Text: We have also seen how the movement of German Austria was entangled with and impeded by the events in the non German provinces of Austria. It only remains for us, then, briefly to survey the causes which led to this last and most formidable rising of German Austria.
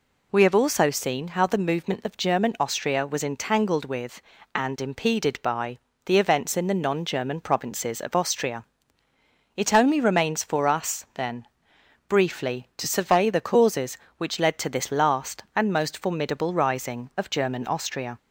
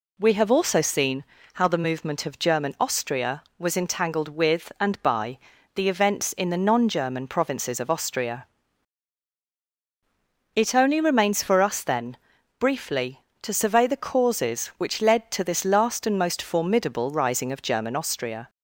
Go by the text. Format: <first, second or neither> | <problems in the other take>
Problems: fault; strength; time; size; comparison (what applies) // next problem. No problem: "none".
first | pauses between "seen" and "how"; slight; at 1.2 s; 0.30 s long // skips "impeded"; at 5.0 s // pauses between "by" and "the"; slight; at 5.3 s; 0.36 s long; slight in the first